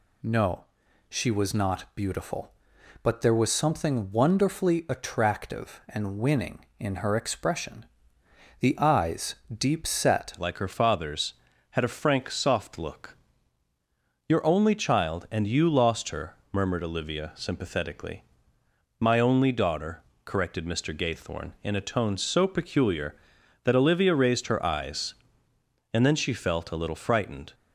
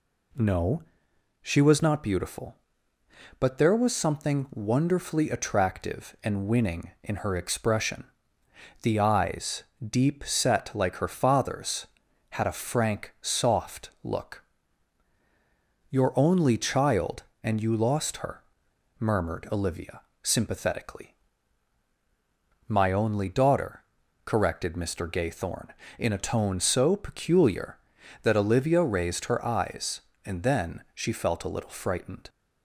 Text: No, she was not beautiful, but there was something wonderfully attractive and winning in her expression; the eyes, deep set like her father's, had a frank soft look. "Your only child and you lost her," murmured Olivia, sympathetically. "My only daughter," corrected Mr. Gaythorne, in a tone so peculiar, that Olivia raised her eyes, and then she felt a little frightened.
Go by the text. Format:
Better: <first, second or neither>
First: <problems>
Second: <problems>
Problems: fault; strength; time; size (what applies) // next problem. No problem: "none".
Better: second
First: changes voice at "like"; from 10.3 s on; 17.2 s long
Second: none